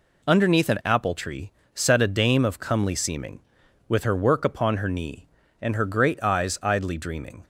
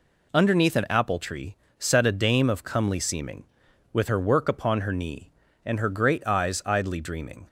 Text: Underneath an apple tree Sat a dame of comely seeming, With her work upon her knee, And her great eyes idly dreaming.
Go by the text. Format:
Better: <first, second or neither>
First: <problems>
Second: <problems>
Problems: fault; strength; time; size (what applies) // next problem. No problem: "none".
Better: neither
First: pauses between "tree" and "Sat"; slight; at 1.5 s; 0.26 s long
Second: pauses between "tree" and "Sat"; slight; at 1.5 s; 0.26 s long